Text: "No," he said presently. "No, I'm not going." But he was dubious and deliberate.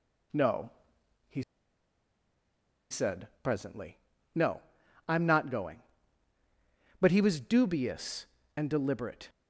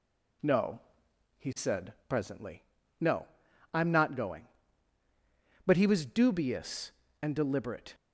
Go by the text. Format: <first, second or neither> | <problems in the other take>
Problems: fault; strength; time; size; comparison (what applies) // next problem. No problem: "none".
second | pauses between "he" and "said"; strong; at 1.4 s; 1.4 s long // pauses between "said" and "presently"; slight; at 3.2 s; 0.16 s long; slight in the second